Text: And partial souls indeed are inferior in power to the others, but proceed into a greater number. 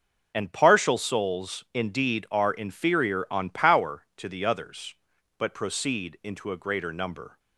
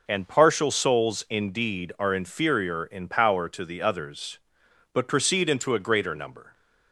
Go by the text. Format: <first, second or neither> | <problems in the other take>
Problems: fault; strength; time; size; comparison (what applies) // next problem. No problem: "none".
second | says "on" for "in"; at 3.3 s